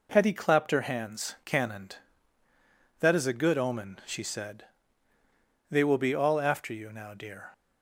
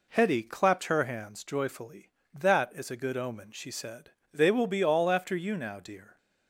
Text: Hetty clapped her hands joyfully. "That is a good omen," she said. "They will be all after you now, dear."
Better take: second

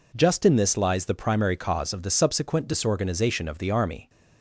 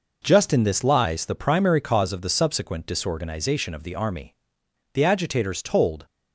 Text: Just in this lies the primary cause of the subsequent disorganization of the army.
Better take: first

